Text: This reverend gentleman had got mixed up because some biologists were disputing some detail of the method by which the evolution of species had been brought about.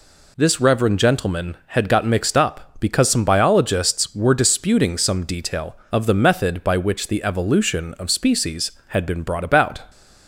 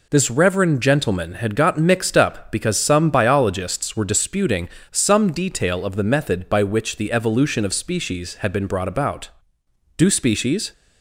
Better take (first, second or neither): first